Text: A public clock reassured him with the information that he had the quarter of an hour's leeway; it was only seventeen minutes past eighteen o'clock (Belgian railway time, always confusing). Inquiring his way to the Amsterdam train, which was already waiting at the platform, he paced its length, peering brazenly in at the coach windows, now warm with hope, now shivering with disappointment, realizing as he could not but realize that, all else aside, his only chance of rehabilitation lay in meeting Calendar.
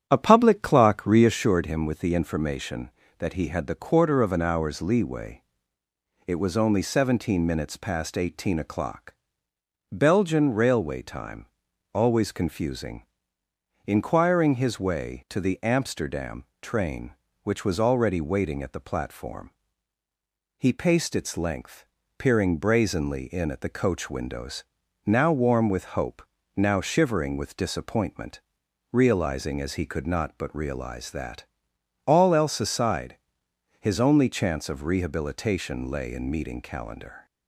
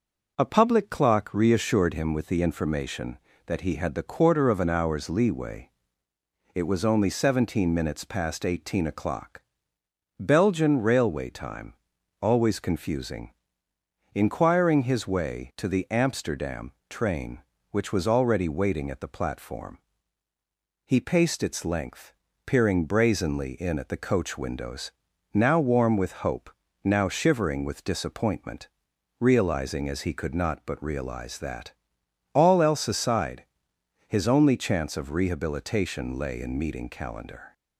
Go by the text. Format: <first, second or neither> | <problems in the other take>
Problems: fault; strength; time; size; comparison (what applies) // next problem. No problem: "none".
second | starts louder than the rest; strong; until 1.4 s; 9.5 dB // pauses between "Amsterdam" and "train"; slight; at 16.4 s; 0.16 s long; slight in the second